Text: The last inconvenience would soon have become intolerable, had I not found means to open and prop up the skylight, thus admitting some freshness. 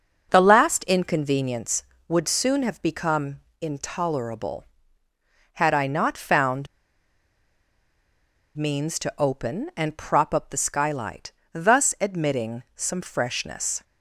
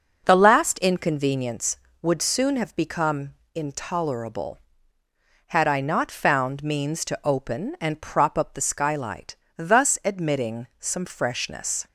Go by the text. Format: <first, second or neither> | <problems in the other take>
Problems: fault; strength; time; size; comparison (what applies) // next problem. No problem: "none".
second | pauses between "become" and "intolerable"; slight; at 3.3 s; 0.22 s long; slight in the second // pauses between "found" and "means"; strong; at 6.6 s; 1.8 s long